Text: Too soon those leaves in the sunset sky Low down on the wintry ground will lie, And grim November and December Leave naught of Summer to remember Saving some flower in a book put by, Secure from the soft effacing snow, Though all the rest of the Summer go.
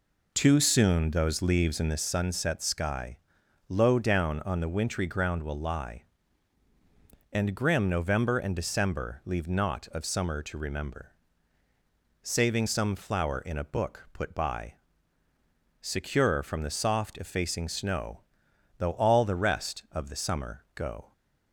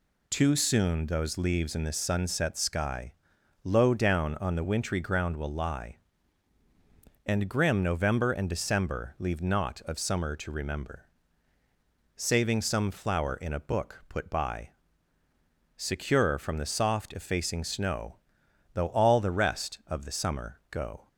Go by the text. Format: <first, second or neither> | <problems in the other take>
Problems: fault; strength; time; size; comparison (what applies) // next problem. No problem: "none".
second | starts louder than the rest; noticeable; until 2.1 s; 4 dB // pauses between "sky" and "Low"; noticeable; at 3.1 s; 0.50 s long; noticeable in the second // pauses between "remember" and "Saving"; at 11.1 s; 1.1 s long; also in the second